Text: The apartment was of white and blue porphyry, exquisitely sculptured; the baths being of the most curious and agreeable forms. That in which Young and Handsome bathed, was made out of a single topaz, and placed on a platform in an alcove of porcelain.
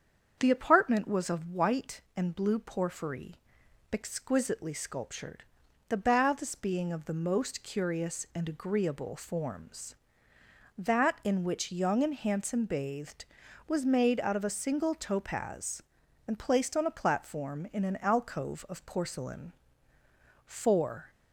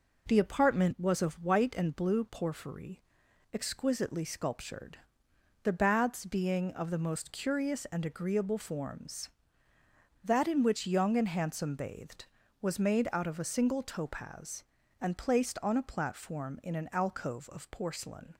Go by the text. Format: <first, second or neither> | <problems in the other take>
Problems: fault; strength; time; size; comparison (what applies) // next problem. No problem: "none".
second | starts louder than the rest; strong; until 1.3 s; 7.5 dB // goes on to say "Four"; noticeable; from 20.4 s on; 0.64 s long